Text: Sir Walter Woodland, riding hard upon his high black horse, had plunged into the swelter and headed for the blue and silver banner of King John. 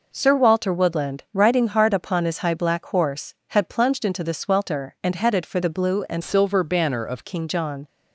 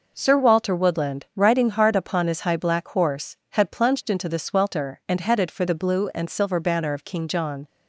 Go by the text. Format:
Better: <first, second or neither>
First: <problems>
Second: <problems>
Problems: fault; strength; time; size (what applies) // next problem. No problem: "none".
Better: second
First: changes voice from "silver" to "of"; from 6.2 to 7.2 s; 1.0 s long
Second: none